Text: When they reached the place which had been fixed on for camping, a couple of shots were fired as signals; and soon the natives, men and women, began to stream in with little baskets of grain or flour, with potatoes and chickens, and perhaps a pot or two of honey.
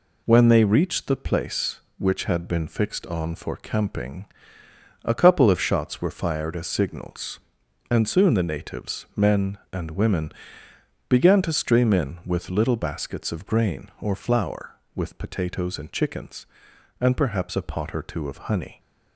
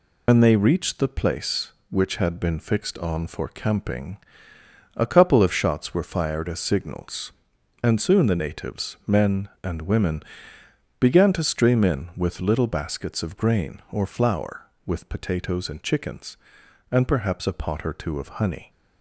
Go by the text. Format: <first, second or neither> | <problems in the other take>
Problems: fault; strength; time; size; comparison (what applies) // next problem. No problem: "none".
first | loses the start of "When"; at 0.2 s; 105 ms